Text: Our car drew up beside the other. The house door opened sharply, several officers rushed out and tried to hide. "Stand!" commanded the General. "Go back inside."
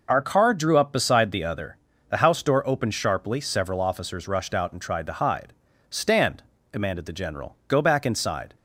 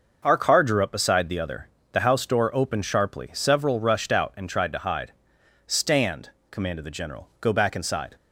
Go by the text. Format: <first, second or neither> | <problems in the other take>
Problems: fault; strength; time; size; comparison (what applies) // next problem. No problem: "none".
first | starts louder than the rest; noticeable; until 1.2 s; 6 dB // skips "officers"; at 3.8 s